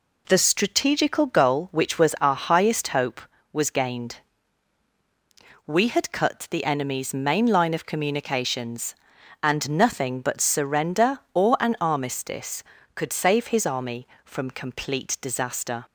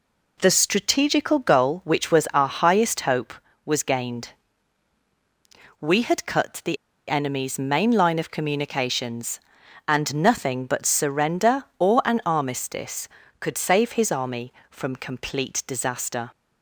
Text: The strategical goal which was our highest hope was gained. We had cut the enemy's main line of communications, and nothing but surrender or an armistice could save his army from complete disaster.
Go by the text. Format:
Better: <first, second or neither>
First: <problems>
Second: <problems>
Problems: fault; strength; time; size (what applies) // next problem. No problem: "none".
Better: first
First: none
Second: pauses between "the" and "enemy's"; slight; at 6.7 s; 0.33 s long